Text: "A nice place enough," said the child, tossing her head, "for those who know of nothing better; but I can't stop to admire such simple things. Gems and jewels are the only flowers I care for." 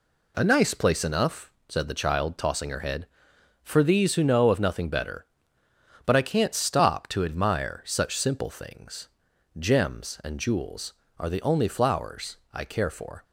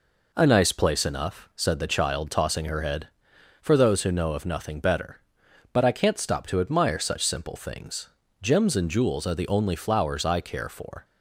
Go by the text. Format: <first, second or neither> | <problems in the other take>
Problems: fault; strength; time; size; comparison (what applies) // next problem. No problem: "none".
second | says "these" for "those"; at 3.8 s // pauses between "flowers" and "I"; slight; at 12.3 s; 0.16 s long